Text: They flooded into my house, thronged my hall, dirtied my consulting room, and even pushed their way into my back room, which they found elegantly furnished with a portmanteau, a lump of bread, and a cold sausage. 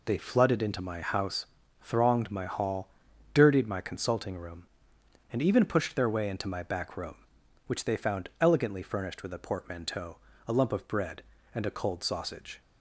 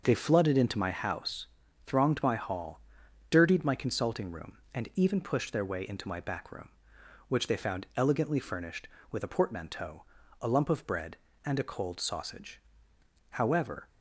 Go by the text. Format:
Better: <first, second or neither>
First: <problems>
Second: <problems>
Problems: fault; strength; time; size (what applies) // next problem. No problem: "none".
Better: first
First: none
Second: starts louder than the rest; noticeable; until 1.0 s; 6 dB // goes on to say "However"; from 13.3 s on; 0.58 s long